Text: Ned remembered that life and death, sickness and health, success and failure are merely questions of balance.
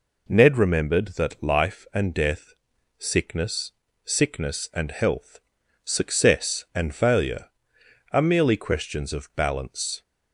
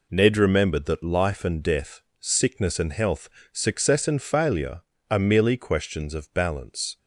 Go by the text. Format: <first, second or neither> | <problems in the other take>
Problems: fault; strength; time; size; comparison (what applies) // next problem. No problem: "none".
second | says "sickness" twice; at 4.0 s